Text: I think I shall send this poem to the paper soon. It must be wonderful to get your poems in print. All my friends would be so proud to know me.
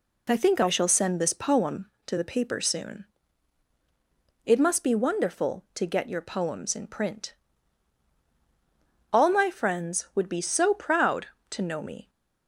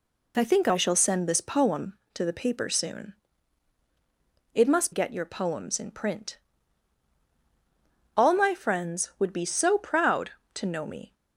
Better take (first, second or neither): first